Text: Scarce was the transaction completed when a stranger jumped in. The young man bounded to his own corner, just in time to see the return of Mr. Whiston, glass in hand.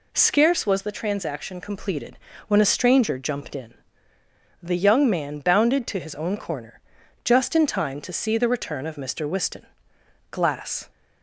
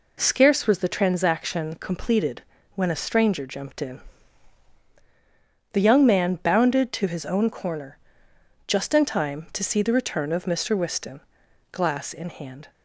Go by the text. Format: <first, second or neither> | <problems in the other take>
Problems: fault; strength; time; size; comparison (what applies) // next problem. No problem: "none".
second | pauses between "completed" and "when"; slight; at 2.1 s; 0.30 s long; slight in the second // stops before "in hand"; at 10.9 s